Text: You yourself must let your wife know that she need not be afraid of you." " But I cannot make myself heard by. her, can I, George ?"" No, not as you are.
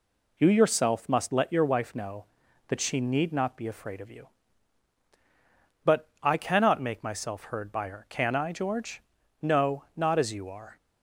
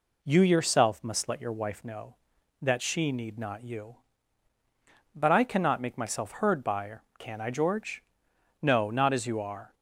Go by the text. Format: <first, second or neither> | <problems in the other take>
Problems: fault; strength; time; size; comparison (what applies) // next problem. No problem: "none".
first | skips "be afraid of"; at 3.6 s